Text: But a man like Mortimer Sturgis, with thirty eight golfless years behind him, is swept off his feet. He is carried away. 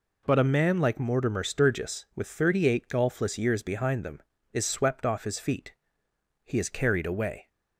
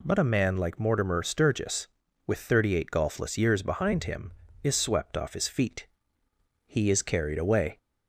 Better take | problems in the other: second | says "them" for "him"; at 4.0 s

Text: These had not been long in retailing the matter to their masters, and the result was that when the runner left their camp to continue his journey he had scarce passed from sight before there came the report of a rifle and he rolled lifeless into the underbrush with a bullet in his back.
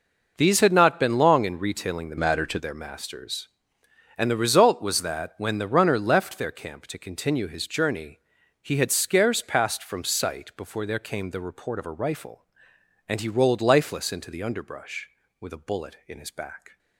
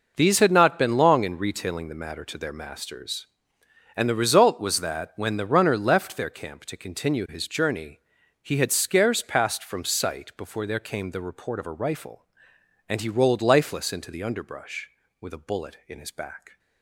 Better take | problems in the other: second | changes voice from "matter" to "to"; from 2.1 to 2.5 s; 0.4 s long // pauses between "journey" and "he"; at 8.1 s; 0.42 s long; also in the second

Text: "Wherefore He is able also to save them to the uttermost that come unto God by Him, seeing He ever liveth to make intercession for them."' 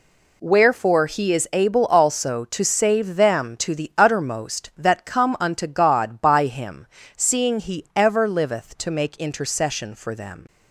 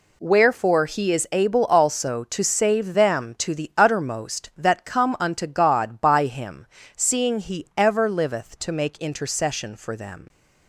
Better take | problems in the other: neither | none

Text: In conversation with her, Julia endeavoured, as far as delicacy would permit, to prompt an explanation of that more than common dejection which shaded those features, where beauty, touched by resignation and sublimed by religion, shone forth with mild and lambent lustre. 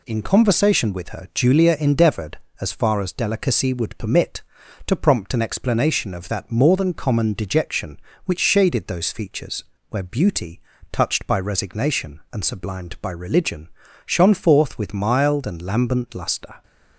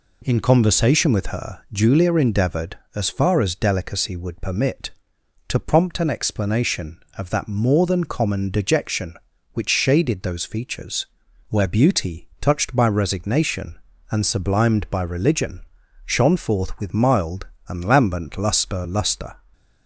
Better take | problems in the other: first | says "lustre" twice; at 18.8 s

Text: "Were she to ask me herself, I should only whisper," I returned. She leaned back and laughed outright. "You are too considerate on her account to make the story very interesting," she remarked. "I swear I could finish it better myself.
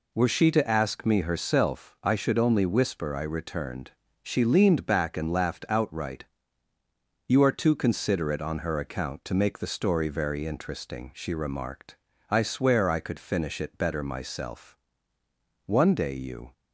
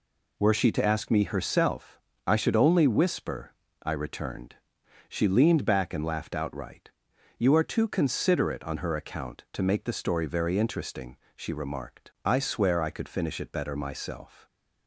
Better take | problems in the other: second | goes on to say "One day you"; noticeable; from 15.6 s on; 0.86 s long

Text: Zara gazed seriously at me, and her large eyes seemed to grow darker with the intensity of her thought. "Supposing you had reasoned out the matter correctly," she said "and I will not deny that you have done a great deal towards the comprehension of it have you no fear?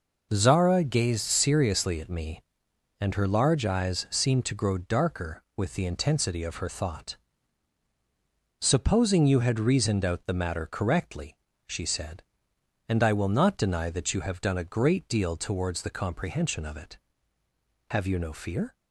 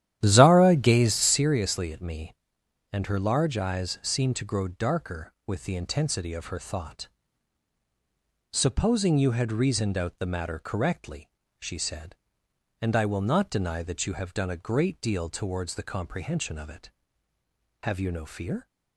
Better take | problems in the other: first | starts louder than the rest; strong; until 1.5 s; 11.5 dB

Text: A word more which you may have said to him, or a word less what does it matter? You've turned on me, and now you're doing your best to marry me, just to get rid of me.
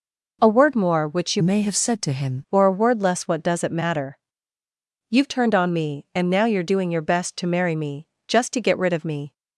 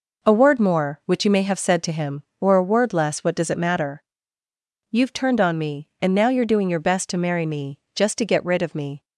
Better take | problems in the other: second | changes voice from "may" to "him"; from 1.3 to 2.4 s; 1.1 s long

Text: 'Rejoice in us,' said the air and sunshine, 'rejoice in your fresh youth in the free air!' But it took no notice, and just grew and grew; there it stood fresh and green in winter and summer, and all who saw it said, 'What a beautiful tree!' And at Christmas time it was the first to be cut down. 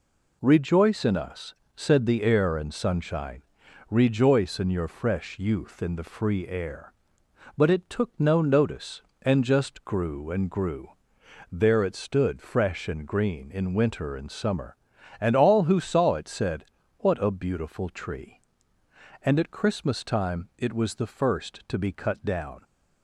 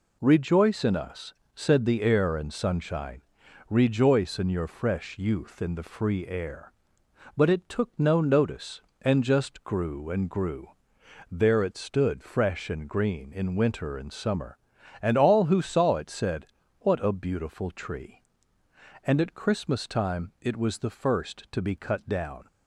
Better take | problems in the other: neither | none

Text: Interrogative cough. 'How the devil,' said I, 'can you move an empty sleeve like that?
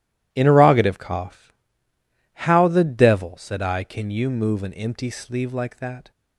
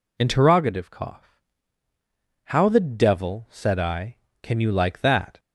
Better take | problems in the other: first | skips "move an empty sleeve"; at 4.7 s

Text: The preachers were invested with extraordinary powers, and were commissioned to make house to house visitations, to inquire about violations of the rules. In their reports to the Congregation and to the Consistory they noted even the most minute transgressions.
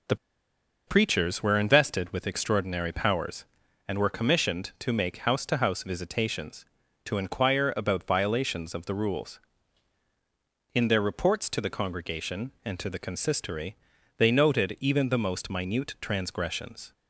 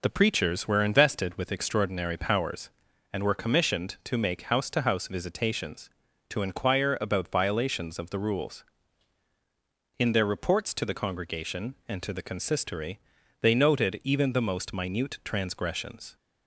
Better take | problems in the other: second | pauses between "The" and "preachers"; noticeable; at 0.1 s; 0.71 s long // pauses between "Consistory" and "they"; at 13.7 s; 0.42 s long; also in the second

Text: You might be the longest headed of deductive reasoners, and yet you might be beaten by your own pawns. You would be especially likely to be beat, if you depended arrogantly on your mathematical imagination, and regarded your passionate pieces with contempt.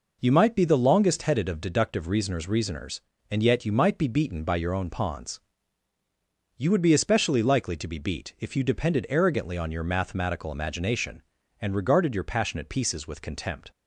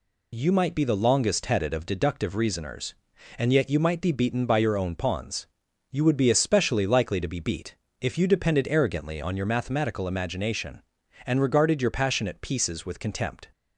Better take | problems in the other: second | says "reasoners" twice; at 2.4 s

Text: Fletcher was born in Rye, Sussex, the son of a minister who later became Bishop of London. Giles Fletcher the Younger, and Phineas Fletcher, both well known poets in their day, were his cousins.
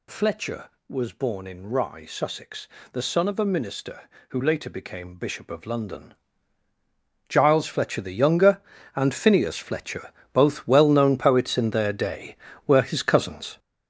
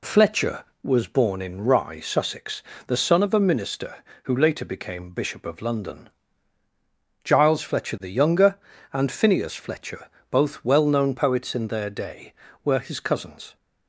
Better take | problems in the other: second | gets louder; strong; throughout; 8 dB

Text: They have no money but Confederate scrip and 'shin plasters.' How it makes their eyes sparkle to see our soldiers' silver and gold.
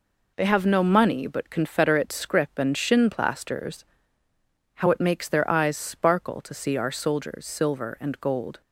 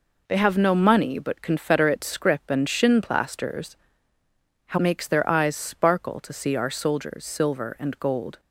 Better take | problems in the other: first | skips "it"; at 4.7 s

